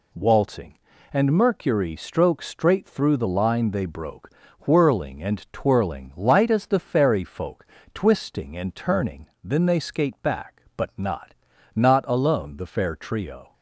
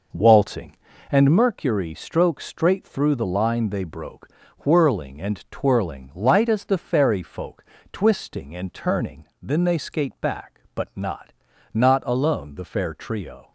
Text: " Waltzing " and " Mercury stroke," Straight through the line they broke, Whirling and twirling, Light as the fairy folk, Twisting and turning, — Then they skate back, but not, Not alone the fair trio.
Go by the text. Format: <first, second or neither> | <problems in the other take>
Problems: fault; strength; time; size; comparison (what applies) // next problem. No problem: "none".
first | starts louder than the rest; noticeable; until 1.4 s; 4.5 dB